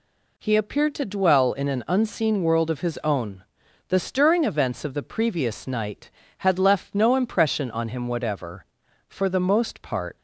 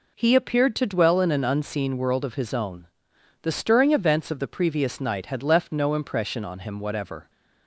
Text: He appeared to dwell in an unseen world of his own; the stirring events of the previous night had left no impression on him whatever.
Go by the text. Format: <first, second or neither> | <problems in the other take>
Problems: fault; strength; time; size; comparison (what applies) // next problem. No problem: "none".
second | goes on to say "For the most part"; noticeable; from 9.0 s on; 1.0 s long